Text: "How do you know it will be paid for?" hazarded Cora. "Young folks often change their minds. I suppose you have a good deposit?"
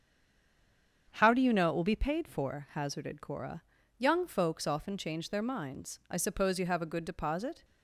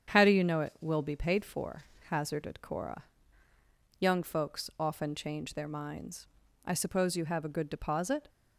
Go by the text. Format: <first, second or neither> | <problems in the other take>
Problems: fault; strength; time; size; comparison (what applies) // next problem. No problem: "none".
second | stays silent before the first word; until 1.0 s; 1.0 s long // starts louder than the rest; strong; until 2.1 s; 8 dB; strong in the second